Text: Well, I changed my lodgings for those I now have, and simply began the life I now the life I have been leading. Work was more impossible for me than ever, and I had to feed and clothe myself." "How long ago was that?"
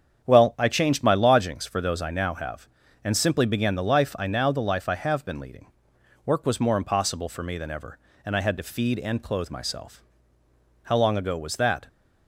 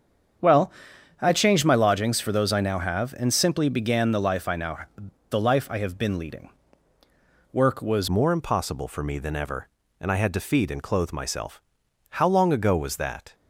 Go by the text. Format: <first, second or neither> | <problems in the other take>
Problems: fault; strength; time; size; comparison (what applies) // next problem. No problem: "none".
first | starts louder than the rest; strong; until 1.9 s; 7.5 dB; strong in the first // pauses between "now" and "the"; noticeable; at 4.7 s; 0.48 s long // changes voice at "more"; from 8.0 s on; 5.3 s long